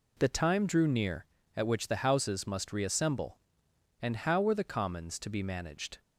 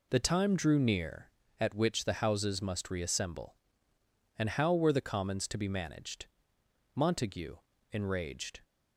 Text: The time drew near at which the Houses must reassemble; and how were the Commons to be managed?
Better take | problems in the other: first | goes on to say "Montague enraged"; strong; from 6.9 s on; 1.6 s long

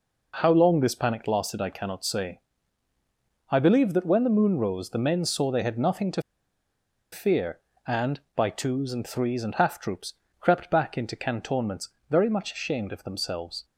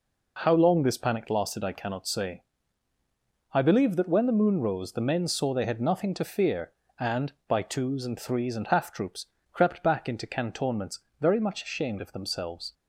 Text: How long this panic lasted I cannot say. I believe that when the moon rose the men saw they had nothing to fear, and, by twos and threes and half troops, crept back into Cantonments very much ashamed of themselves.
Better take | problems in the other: second | pauses between "to" and "fear"; noticeable; at 6.2 s; 0.91 s long // pauses between "Cantonments" and "very"; slight; at 11.8 s; 0.22 s long; slight in the second

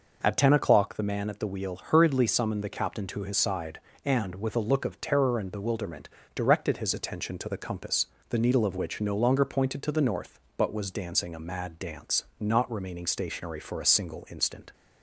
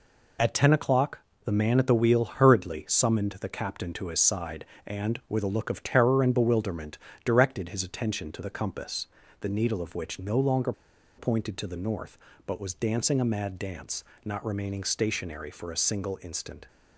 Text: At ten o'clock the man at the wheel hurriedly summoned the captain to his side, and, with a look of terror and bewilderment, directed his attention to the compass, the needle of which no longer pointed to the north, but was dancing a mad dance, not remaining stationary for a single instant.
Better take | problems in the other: first | pauses between "o'clock" and "the"; slight; at 1.1 s; 0.26 s long // pauses between "longer" and "pointed"; at 10.7 s; 0.45 s long

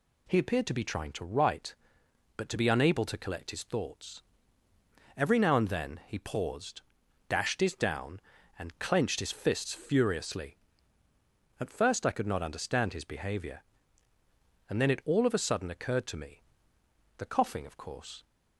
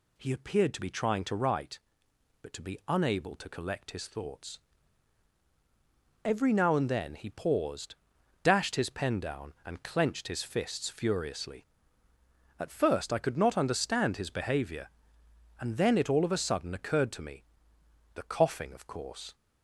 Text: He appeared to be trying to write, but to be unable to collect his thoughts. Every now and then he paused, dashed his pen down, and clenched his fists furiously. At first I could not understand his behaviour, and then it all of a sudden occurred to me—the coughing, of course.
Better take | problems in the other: second | skips "pen"; at 7.7 s

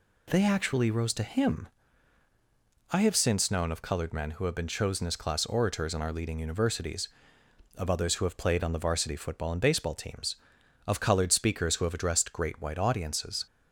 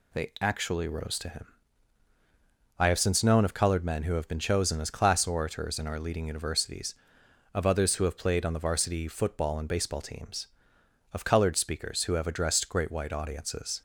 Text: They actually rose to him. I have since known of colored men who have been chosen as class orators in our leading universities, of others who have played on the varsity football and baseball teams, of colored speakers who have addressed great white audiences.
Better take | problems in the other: neither | none

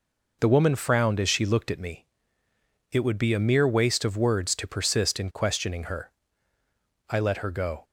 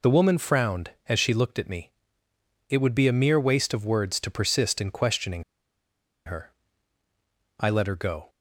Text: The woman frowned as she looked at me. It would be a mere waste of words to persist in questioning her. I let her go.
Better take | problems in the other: first | pauses between "questioning" and "her"; noticeable; at 5.4 s; 0.83 s long

